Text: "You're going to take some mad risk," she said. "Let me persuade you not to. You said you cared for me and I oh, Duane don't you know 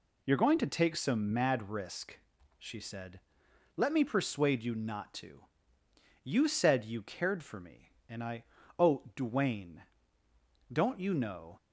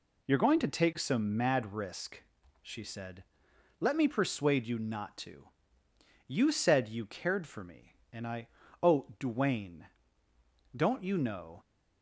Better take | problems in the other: neither | pauses between "I" and "oh"; slight; the same in both // pauses between "Duane" and "don't"; noticeable; the same in both

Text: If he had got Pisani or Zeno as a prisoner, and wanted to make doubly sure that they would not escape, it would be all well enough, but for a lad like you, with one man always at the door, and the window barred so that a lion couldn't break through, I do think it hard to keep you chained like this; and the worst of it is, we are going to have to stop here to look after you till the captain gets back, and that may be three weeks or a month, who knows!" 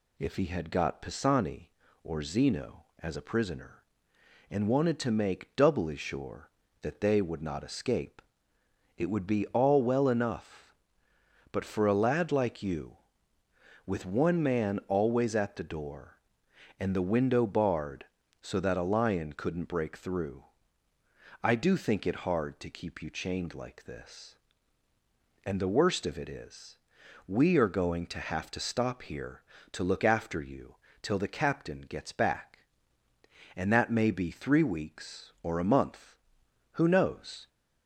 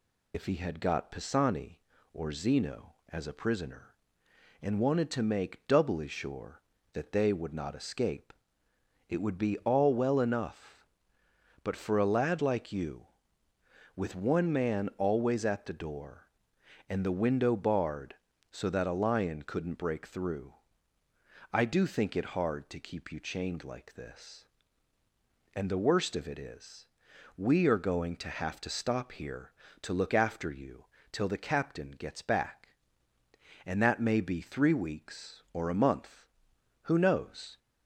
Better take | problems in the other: first | loses the start of "If"; at 0.3 s; 65 ms // pauses between "you" and "till"; slight; at 30.8 s; 0.26 s long; slight in the first

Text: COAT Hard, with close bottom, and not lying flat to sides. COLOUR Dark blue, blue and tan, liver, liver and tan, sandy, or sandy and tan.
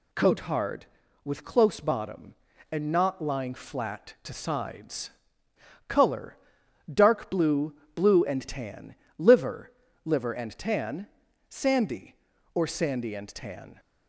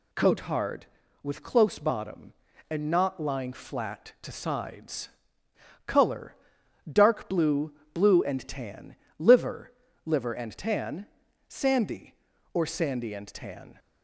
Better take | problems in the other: neither | pauses between "COLOUR" and "Dark"; noticeable; the same in both

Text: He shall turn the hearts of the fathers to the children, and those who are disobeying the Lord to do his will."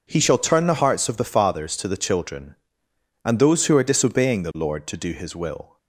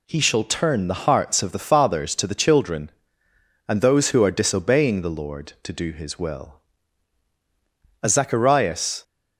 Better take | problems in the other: first | goes on to say "As Zacharias"; noticeable; from 8.0 s on; 1.0 s long

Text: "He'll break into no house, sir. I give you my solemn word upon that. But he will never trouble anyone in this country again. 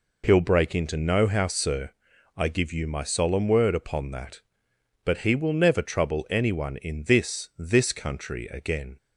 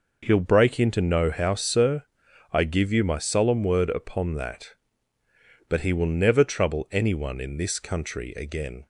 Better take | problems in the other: second | says "this" twice; at 7.5 s

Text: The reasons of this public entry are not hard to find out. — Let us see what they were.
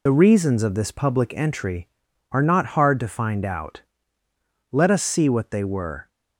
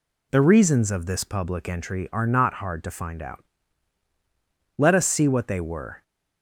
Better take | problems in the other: second | loses the start of "The"; at 0.0 s; 40 ms

